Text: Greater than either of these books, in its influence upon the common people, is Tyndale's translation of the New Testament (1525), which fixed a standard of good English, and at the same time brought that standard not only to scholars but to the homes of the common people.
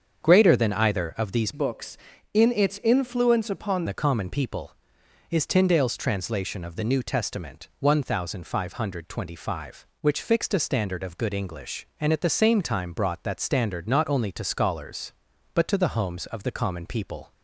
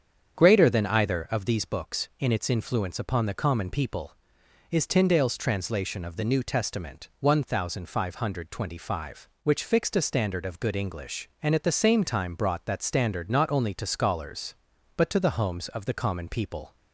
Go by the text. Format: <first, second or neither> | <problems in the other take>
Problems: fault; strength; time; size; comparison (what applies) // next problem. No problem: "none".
second | starts louder than the rest; strong; until 1.2 s; 7 dB; strong in the second // changes voice from "books" to "upon"; from 1.5 to 3.8 s; 2.3 s long